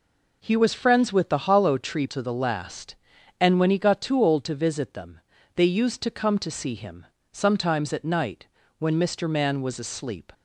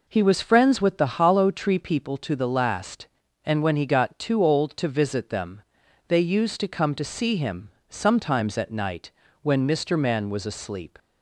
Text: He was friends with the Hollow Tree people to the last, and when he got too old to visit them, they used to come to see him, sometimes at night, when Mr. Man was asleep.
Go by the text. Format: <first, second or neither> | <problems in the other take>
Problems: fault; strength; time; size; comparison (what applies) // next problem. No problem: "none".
second | skips "people"; at 2.0 s